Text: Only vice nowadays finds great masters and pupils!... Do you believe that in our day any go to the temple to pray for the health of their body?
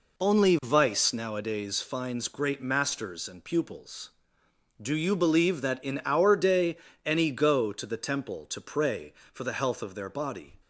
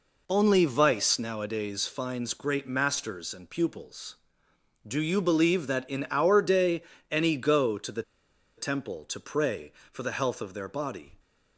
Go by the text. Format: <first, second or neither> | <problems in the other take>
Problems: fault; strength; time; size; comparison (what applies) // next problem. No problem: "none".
first | pauses between "day" and "any"; slight; at 6.8 s; 0.30 s long; slight in the first // pauses between "the" and "temple"; noticeable; at 8.0 s; 0.56 s long